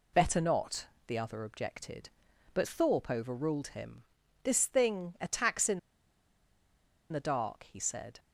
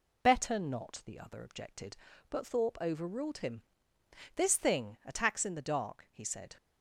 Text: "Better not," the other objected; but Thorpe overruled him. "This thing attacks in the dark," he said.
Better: second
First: pauses between "in" and "the"; strong; at 5.7 s; 1.3 s long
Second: none

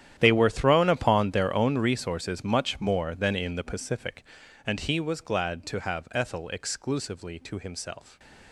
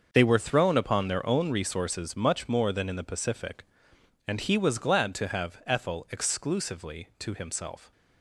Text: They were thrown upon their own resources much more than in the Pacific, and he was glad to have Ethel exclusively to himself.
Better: second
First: gets quieter; strong; throughout; 17 dB // starts louder than the rest; strong; until 1.1 s; 10.5 dB // stays silent after the last word; slight; from 7.9 s on; 0.6 s long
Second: starts louder than the rest; until 1.1 s; 6.5 dB

